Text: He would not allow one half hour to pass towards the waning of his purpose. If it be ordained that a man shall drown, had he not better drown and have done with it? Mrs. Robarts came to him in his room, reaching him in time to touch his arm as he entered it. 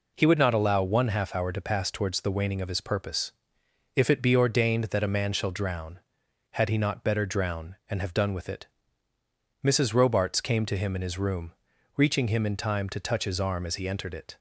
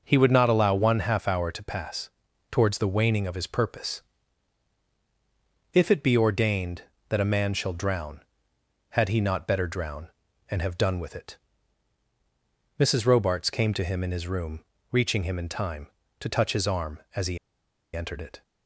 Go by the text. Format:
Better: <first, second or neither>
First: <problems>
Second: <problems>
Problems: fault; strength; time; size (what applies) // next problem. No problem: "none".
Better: first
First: none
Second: pauses between "pass" and "towards"; at 2.1 s; 0.40 s long // pauses between "he" and "entered"; noticeable; at 17.3 s; 0.57 s long